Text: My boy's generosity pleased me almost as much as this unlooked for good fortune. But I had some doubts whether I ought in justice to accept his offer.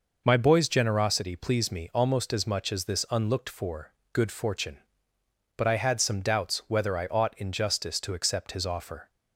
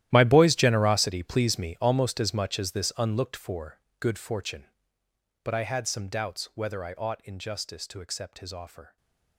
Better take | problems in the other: first | gets quieter; strong; throughout; 17 dB // pauses between "for" and "good"; slight; at 3.8 s; 0.18 s long; slight in the first // stays silent after the last word; slight; from 8.8 s on; 0.5 s long

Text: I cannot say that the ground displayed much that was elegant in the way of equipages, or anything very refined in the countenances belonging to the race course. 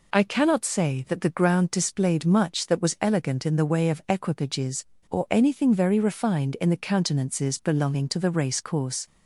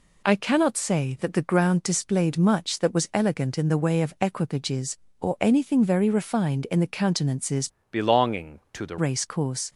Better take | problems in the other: first | changes voice from "belonging" to "the"; from 7.9 to 8.9 s; 1.0 s long

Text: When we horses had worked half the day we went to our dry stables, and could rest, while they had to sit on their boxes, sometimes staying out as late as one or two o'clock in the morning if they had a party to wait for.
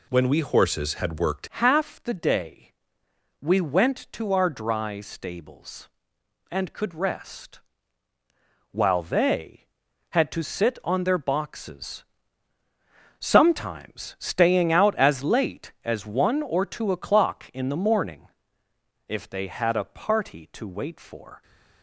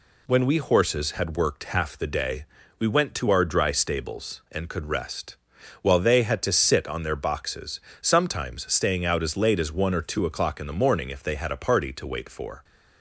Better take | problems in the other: second | changes voice at "half"; from 1.4 s on; 20.0 s long // pauses between "day" and "we"; noticeable; at 2.7 s; 0.70 s long; slight in the second // pauses between "morning" and "if"; noticeable; at 18.2 s; 0.80 s long

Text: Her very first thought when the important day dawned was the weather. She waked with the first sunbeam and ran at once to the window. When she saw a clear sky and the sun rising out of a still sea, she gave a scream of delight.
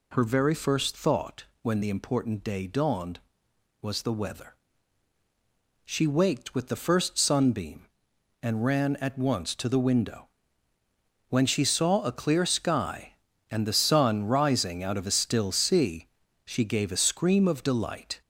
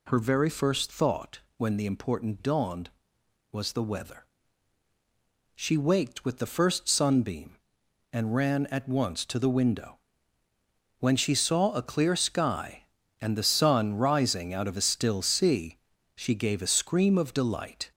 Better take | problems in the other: first | pauses between "thought" and "when"; slight; at 1.3 s; 0.18 s long; slight in the first // skips "day"; at 2.3 s

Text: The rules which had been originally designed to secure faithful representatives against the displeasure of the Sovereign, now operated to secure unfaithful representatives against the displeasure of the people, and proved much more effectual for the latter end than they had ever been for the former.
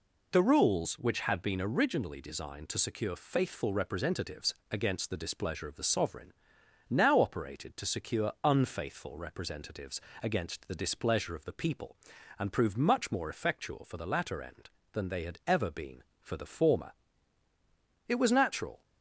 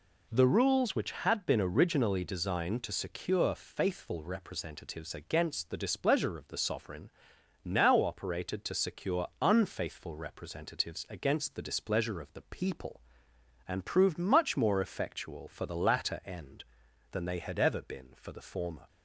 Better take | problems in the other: second | pauses between "representatives" and "against"; slight; at 4.5 s; 0.16 s long // pauses between "representatives" and "against"; slight; at 9.9 s; 0.24 s long // goes on to say "It was natural"; noticeable; from 18.0 s on; 0.78 s long

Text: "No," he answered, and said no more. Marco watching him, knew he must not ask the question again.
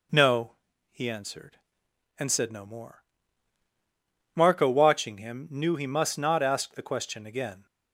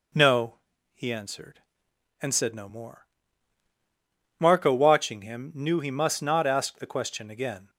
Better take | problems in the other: neither | none

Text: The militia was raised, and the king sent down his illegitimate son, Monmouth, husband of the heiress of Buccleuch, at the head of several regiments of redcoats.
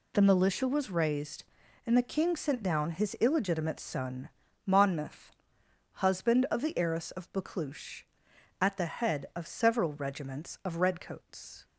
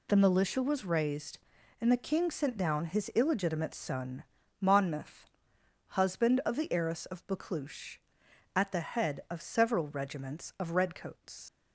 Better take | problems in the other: first | leaves "redcoats" unfinished; at 11.4 s; 105 ms

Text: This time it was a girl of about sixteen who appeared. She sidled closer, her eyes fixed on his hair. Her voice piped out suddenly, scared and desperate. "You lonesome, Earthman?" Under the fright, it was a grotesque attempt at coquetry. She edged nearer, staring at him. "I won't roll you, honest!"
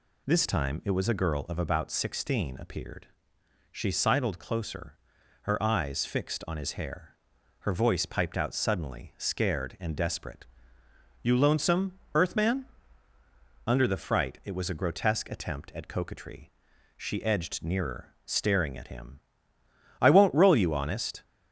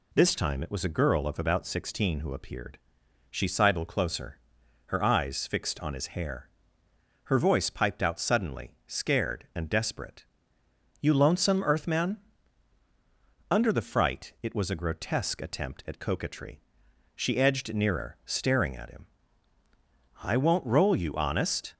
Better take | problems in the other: second | skips "who"; at 2.5 s

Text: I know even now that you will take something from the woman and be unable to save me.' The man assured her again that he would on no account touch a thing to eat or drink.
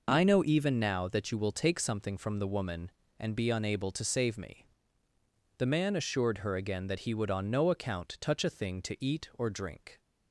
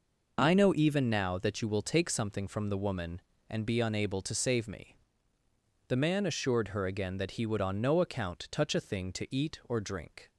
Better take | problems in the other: neither | none

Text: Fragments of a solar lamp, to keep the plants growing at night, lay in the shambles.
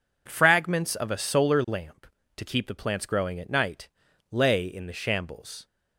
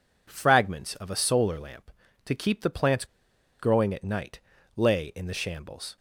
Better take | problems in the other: first | pauses between "plants" and "growing"; noticeable; at 3.0 s; 0.54 s long

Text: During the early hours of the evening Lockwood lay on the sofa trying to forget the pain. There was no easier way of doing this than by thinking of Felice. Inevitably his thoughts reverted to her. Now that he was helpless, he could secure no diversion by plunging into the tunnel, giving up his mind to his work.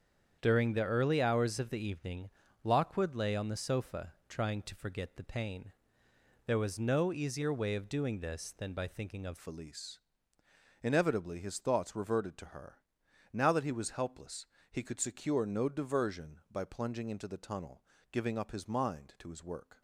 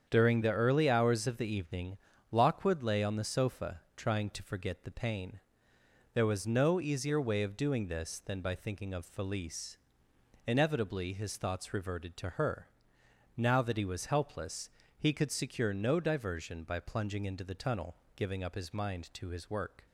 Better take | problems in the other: second | starts louder than the rest; strong; until 1.4 s; 8 dB; strong in the second // pauses between "evening" and "Lockwood"; slight; at 2.3 s; 0.32 s long; slight in the second // pauses between "sofa" and "trying"; slight; at 4.1 s; 0.16 s long; slight in the second // changes voice at "Felice"; from 9.3 s on; 10.5 s long

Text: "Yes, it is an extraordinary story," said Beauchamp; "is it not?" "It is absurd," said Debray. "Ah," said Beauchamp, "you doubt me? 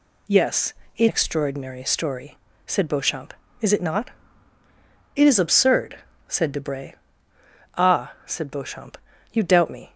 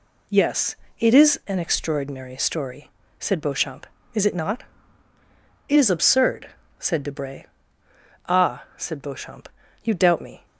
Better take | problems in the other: second | skips "is an"; at 1.0 s

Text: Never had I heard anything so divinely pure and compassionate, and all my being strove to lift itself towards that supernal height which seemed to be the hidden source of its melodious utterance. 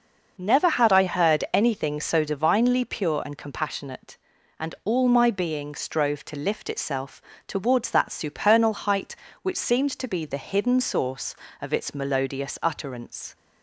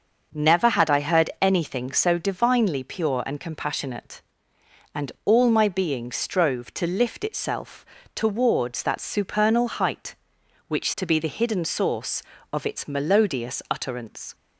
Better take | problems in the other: first | pauses between "itself" and "towards"; slight; at 7.8 s; 0.30 s long; slight in the first // skips "seemed"; at 10.9 s

